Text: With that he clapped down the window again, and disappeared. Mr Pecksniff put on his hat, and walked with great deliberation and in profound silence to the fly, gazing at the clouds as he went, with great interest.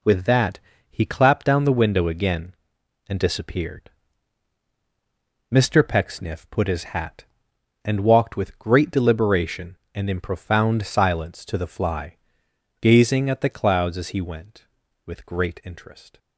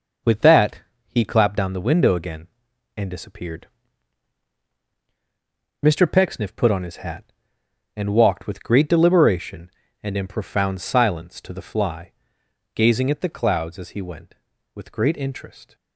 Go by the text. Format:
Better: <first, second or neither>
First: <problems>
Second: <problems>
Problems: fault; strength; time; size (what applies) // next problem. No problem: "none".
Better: second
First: pauses between "that" and "he"; slight; at 0.5 s; 0.32 s long // skips "on"; at 6.6 s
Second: pauses between "that" and "he"; slight; at 0.8 s; 0.26 s long